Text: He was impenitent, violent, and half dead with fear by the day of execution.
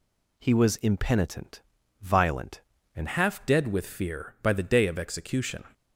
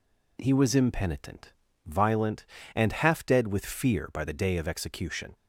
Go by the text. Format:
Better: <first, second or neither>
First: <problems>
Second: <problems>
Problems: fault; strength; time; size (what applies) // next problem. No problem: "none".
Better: second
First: changes voice at "half"; from 3.0 s on; 2.6 s long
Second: none